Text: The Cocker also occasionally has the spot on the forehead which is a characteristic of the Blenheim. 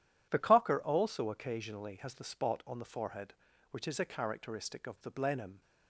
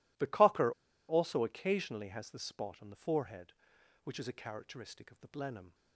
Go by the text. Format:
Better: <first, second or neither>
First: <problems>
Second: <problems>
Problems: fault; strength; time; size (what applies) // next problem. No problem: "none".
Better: first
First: none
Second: pauses between "Cocker" and "also"; at 0.7 s; 0.37 s long